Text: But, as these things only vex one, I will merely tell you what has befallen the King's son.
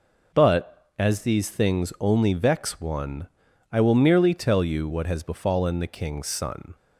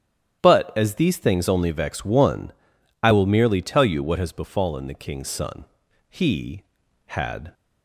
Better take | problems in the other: first | starts louder than the rest; strong; until 1.4 s; 10 dB // goes on to say "He had"; from 6.0 s on; 1.4 s long

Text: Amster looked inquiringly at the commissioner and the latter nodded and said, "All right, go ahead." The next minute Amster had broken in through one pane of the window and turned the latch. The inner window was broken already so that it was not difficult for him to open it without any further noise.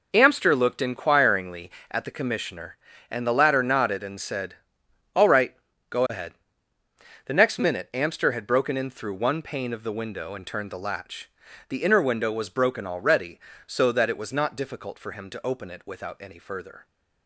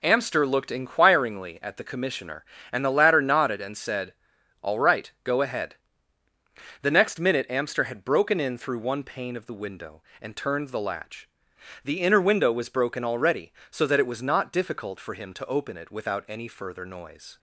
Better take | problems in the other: second | stops before "noise"; at 16.8 s

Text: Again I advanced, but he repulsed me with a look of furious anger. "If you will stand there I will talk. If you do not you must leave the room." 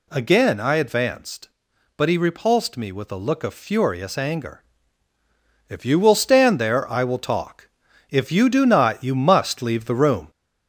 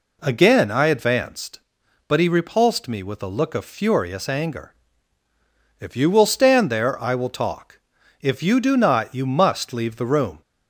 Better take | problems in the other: second | gets louder; slight; throughout; 2.5 dB

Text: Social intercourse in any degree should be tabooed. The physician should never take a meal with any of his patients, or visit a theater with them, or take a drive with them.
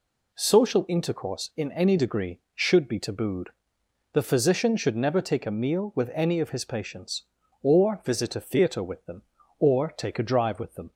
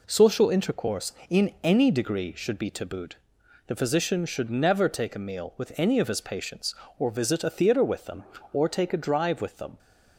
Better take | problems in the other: neither | none

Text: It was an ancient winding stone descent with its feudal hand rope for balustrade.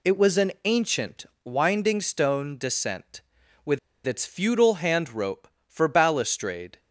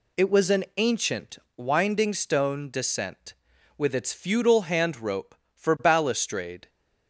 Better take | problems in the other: second | pauses between "ancient" and "winding"; slight; at 1.2 s; 0.18 s long; slight in the second // pauses between "with" and "its"; slight; at 3.7 s; 0.28 s long

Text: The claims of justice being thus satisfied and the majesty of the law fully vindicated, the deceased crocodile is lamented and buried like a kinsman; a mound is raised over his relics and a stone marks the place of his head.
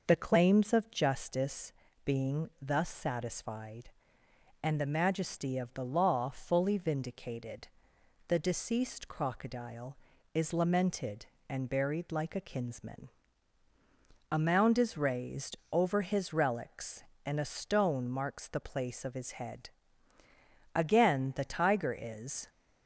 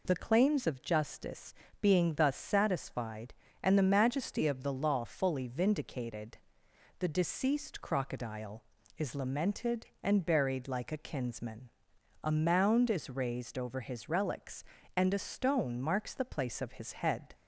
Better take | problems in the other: second | pauses between "justice" and "being"; slight; at 1.7 s; 0.32 s long; slight in the second // pauses between "raised" and "over"; slight; at 15.5 s; 0.16 s long // goes on to say "Again the tiger is"; strong; from 20.7 s on; 1.7 s long

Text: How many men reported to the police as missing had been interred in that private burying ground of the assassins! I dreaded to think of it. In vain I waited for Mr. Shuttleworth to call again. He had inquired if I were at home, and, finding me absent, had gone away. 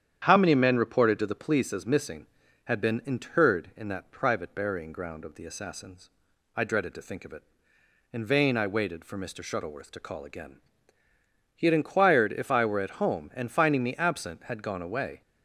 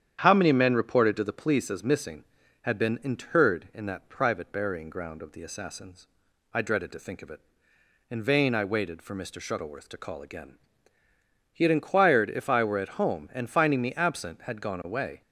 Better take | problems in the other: neither | starts louder than the rest; strong; the same in both

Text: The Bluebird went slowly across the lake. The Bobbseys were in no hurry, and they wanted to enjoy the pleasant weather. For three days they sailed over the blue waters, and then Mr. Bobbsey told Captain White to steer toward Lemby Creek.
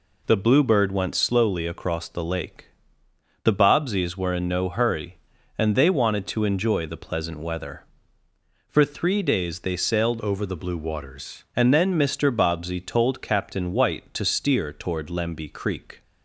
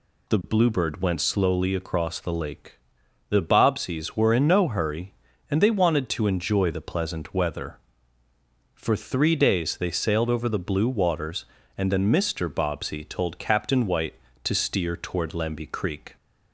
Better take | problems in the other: second | changes voice from "over" to "waters"; from 10.1 to 11.4 s; 1.3 s long

